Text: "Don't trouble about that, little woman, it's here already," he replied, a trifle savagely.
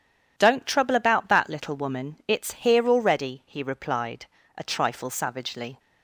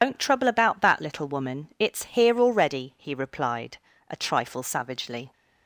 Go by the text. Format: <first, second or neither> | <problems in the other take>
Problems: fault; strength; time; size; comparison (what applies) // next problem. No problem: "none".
first | loses the start of "Don't"; at 0.0 s; 95 ms